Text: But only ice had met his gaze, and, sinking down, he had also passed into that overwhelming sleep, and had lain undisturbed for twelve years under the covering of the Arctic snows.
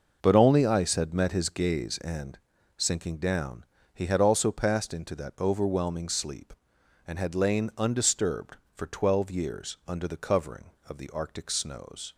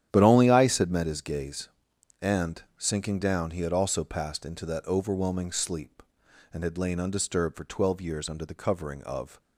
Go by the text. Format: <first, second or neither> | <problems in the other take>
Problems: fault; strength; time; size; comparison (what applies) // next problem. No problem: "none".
first | starts louder than the rest; strong; until 1.1 s; 10.5 dB // stops before "the Arctic snows"; at 9.3 s